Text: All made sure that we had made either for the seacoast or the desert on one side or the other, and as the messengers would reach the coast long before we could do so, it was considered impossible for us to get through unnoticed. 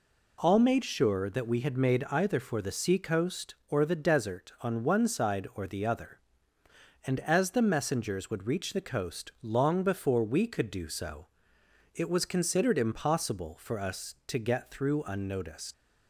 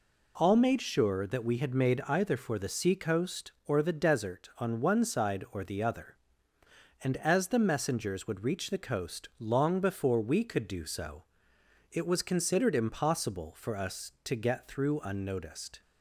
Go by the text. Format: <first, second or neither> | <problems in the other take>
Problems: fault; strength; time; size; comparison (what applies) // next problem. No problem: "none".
second | leaves "unnoticed" unfinished; at 15.7 s; 95 ms